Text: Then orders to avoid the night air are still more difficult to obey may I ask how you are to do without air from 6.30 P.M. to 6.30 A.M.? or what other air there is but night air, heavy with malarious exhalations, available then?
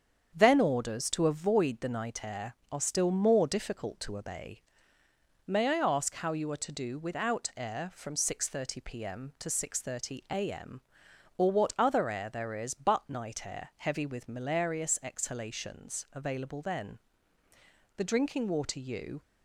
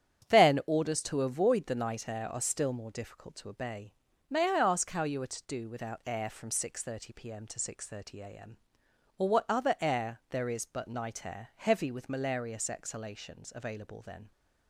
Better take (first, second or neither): second